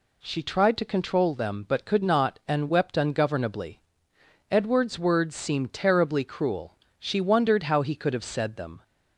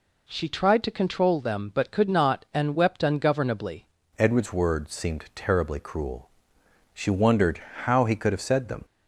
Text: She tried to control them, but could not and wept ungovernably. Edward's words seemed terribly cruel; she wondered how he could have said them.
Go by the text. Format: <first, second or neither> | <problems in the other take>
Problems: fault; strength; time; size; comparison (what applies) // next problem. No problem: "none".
first | changes voice at "Edward's"; from 4.1 s on; 4.7 s long // pauses between "wondered" and "how"; slight; at 7.6 s; 0.22 s long